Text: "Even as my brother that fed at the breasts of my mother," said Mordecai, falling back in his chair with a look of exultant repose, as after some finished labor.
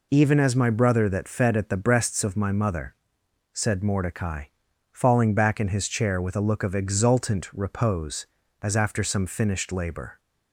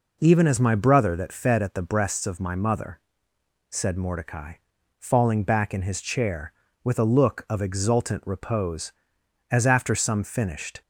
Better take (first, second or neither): first